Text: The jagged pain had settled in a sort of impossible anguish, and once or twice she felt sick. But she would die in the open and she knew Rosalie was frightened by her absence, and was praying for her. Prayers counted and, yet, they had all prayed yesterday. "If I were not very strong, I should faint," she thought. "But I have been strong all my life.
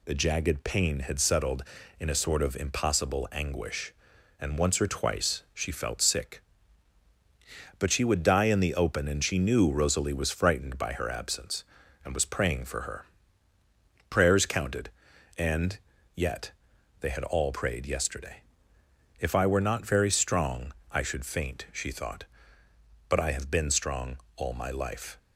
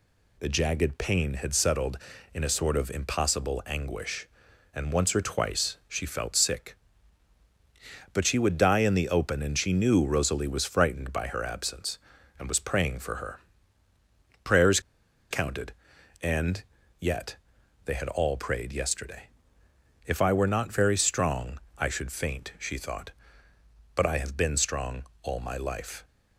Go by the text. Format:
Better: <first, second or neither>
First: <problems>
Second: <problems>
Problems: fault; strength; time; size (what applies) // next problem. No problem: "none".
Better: first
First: pauses between "strong" and "all"; slight; at 24.1 s; 0.18 s long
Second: pauses between "Prayers" and "counted"; noticeable; at 14.7 s; 0.51 s long // pauses between "strong" and "all"; slight; at 25.0 s; 0.18 s long